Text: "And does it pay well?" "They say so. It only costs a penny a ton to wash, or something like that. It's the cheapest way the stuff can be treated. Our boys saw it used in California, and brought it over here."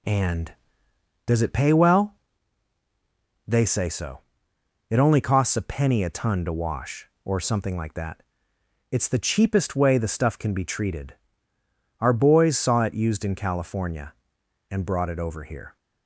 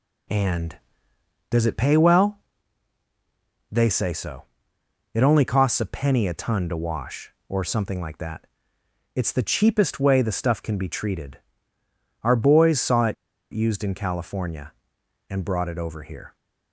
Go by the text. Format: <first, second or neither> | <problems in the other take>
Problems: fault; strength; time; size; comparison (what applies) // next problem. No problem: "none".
first | pauses between "it" and "used"; at 13.1 s; 0.38 s long